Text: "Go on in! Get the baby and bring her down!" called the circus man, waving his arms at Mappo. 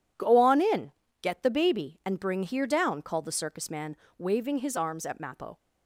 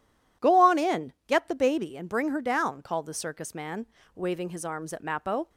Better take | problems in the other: second | says "here" for "her"; at 2.4 s

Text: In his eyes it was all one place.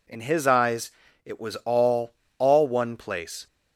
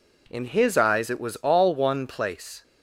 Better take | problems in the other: second | pauses between "eyes" and "it"; slight; at 0.9 s; 0.34 s long // says "all" twice; at 2.3 s

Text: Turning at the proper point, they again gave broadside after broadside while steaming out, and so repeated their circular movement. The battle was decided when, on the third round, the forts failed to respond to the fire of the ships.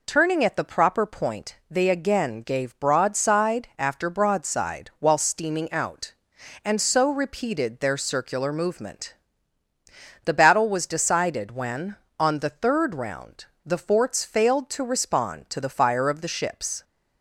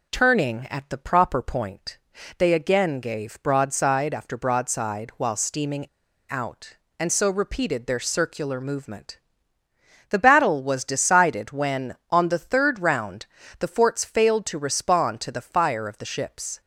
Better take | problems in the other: first | pauses between "steaming" and "out"; at 5.8 s; 0.44 s long

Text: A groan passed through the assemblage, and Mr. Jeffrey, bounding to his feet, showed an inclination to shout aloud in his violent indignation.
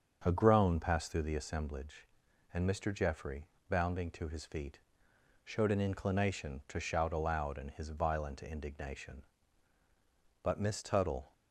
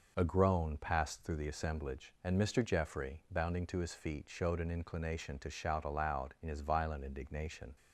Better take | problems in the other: second | starts louder than the rest; until 1.2 s; 7 dB // goes on to say "But Miss Tuttle"; noticeable; from 10.4 s on; 0.88 s long

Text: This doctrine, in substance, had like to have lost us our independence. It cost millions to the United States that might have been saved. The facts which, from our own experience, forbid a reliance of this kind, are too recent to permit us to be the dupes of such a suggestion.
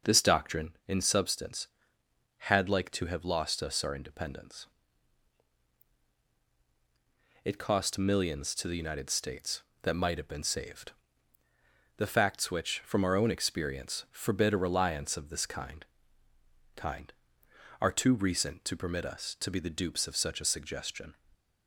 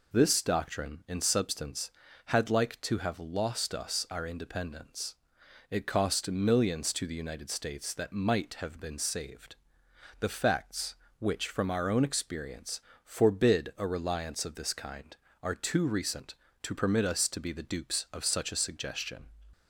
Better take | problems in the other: second | starts louder than the rest; until 1.1 s; 6 dB // says "kind" twice; at 16.7 s

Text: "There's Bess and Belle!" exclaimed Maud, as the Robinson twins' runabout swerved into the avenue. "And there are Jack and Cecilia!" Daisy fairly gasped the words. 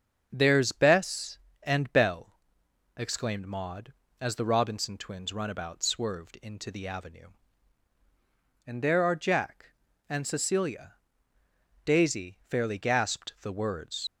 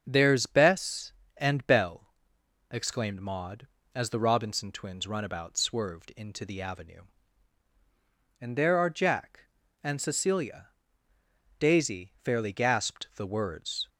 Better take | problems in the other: second | starts louder than the rest; strong; until 1.3 s; 7 dB; also in the second // leaves "words" unfinished; at 14.0 s; 70 ms

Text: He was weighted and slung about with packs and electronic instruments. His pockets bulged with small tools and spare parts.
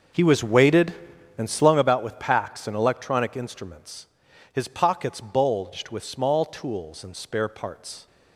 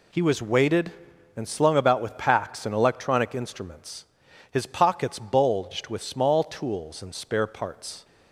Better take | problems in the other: second | starts louder than the rest; until 1.9 s; 6 dB

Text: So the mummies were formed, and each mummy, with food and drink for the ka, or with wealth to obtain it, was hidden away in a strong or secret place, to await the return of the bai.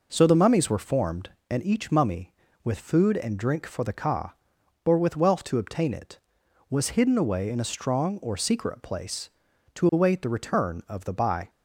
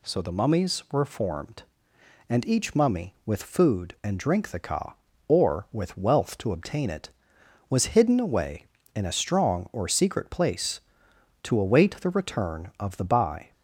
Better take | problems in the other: first | skips "for"; at 4.5 s

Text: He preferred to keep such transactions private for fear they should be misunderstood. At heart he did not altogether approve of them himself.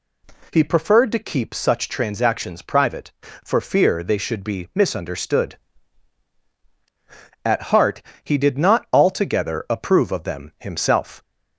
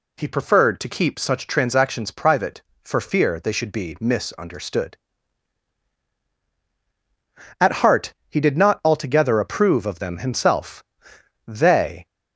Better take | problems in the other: first | pauses between "heart" and "he"; slight; at 8.1 s; 0.16 s long; slight in the first // goes on to say "They"; from 11.4 s on; 0.58 s long

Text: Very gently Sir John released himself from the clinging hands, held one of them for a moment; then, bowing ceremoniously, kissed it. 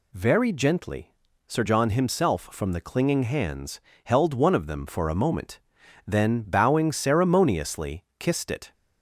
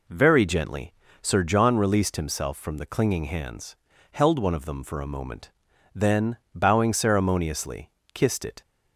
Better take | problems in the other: second | pauses between "gently" and "Sir"; slight; at 1.1 s; 0.34 s long; slight in the second // skips "released"; at 1.8 s

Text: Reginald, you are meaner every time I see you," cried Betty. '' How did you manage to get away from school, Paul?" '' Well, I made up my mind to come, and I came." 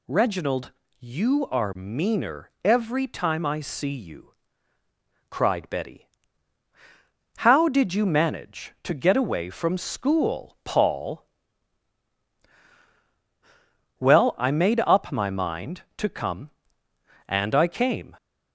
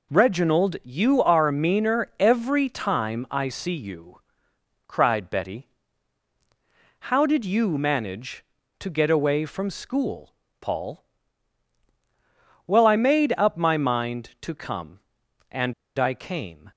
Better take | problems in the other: first | pauses between "and" and "I"; slight; at 15.7 s; 0.23 s long

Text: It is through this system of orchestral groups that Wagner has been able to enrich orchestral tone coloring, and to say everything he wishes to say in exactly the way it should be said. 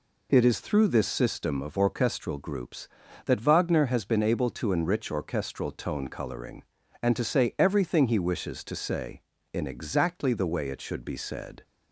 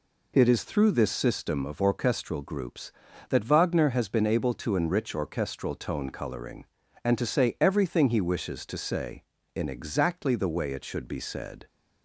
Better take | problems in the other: neither | none

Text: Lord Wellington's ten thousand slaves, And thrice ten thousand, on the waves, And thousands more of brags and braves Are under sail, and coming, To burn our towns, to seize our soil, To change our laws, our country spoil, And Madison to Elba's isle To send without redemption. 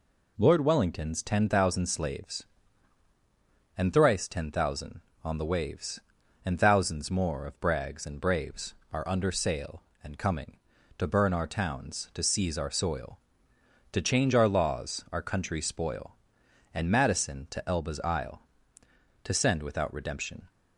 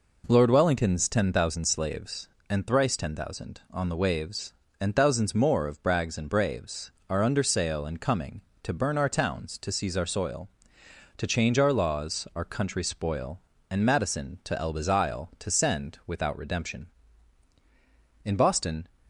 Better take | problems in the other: first | goes on to say "In Boston"; noticeable; from 18.2 s on; 0.64 s long

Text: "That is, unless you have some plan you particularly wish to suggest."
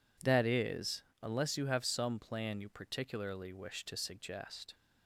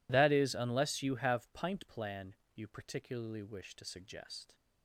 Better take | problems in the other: first | says "pint" for "some"; at 1.5 s // pauses between "plan" and "you"; slight; at 2.3 s; 0.18 s long

